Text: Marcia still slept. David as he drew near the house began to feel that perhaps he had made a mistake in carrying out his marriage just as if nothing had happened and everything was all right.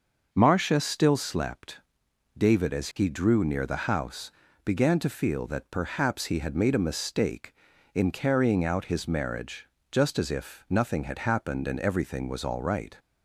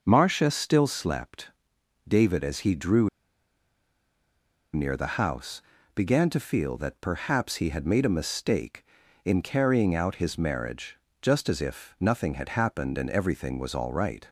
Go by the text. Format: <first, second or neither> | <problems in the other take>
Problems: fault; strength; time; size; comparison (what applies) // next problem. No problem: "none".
first | starts louder than the rest; until 1.0 s; 6 dB; also in the first // pauses between "drew" and "near"; strong; at 3.0 s; 1.6 s long // pauses between "house" and "began"; slight; at 5.6 s; 0.34 s long; slight in the first // pauses between "marriage" and "just"; slight; at 10.9 s; 0.24 s long; slight in the first